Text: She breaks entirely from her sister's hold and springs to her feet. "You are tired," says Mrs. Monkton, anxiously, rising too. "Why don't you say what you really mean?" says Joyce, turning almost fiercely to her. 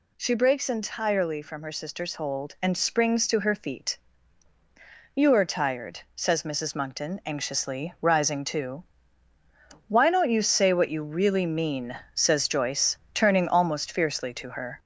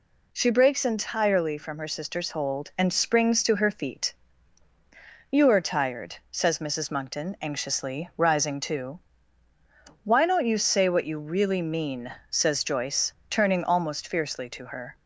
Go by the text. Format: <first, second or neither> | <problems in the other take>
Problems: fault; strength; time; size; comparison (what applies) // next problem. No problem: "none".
second | gets louder; noticeable; throughout; 4 dB